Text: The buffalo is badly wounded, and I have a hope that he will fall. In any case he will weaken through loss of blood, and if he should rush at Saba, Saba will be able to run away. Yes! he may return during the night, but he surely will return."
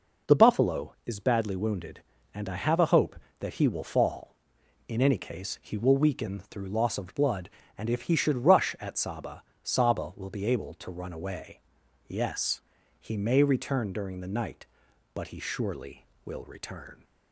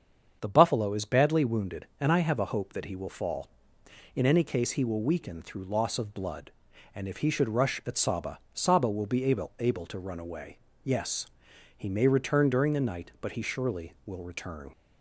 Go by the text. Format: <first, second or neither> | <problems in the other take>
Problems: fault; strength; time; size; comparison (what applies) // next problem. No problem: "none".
first | starts louder than the rest; strong; until 1.4 s; 7.5 dB // says "able" twice; at 9.5 s